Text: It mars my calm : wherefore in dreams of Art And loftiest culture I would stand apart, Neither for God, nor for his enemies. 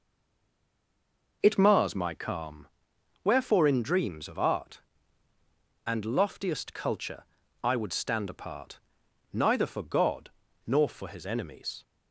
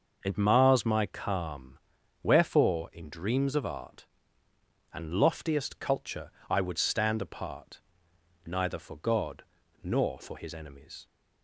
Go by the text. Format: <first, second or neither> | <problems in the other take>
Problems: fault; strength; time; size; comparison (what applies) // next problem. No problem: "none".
second | stays silent before the first word; noticeable; until 1.4 s; 1.4 s long // pauses between "culture" and "I"; at 7.2 s; 0.38 s long; slight in the second